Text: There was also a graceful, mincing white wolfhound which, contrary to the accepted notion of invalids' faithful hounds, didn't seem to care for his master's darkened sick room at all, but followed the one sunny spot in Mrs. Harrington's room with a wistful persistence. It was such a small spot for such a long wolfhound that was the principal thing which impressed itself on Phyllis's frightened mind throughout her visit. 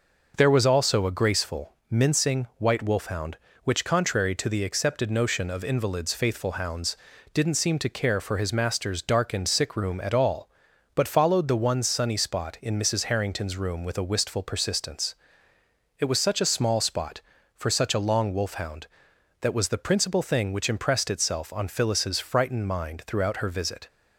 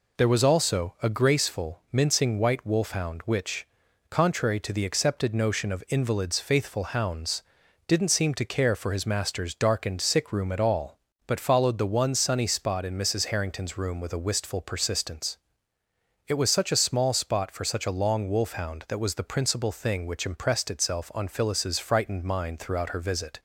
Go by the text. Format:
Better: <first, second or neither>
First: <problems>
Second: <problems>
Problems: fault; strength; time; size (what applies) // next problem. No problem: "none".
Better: neither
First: none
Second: none